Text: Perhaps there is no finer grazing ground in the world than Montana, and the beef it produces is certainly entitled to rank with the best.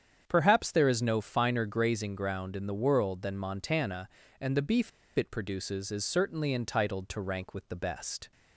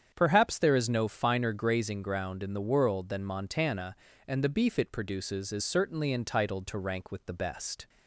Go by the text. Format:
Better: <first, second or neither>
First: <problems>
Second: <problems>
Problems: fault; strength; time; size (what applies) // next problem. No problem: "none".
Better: second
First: starts louder than the rest; strong; until 1.2 s; 8 dB // pauses between "beef" and "it"; slight; at 4.9 s; 0.27 s long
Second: starts louder than the rest; strong; until 1.1 s; 8 dB